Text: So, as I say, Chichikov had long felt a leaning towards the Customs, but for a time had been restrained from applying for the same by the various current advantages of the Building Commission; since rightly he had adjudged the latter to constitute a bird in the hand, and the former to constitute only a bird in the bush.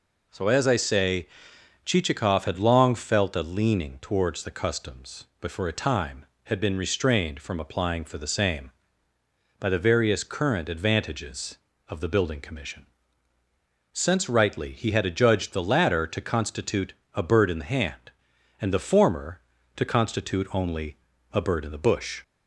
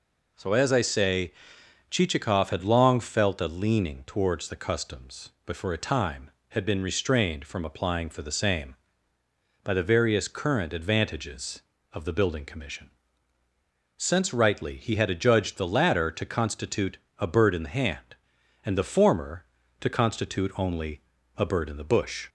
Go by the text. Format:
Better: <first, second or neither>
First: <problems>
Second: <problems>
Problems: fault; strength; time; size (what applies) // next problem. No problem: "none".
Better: neither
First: pauses between "constitute" and "a"; slight; at 16.9 s; 0.22 s long // pauses between "only" and "a"; slight; at 20.9 s; 0.34 s long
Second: pauses between "constitute" and "a"; slight; at 16.9 s; 0.22 s long // pauses between "only" and "a"; slight; at 21.0 s; 0.34 s long